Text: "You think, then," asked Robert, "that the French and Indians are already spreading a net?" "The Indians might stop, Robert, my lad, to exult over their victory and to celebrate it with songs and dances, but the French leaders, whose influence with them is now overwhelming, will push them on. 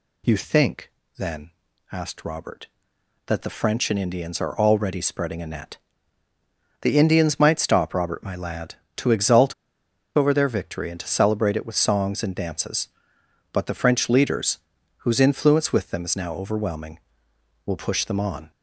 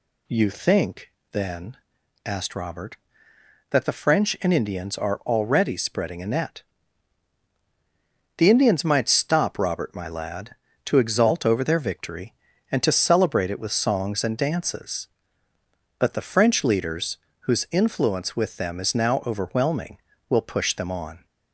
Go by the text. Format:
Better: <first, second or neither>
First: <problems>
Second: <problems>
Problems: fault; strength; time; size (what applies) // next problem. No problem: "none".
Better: second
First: pauses between "exult" and "over"; noticeable; at 9.5 s; 0.62 s long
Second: none